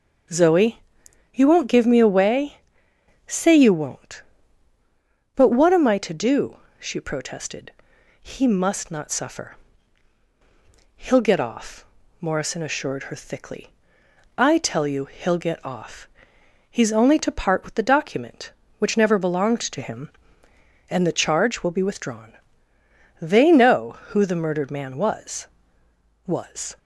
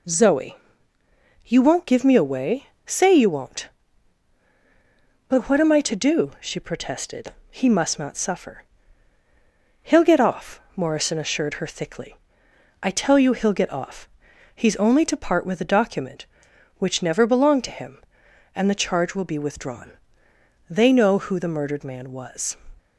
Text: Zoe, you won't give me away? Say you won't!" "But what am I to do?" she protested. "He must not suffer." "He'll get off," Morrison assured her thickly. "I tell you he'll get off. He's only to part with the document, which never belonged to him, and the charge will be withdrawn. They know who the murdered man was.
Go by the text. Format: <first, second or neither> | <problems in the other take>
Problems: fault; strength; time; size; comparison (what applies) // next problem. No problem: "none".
second | starts louder than the rest; until 1.8 s; 6 dB // says "was" twice; at 26.2 s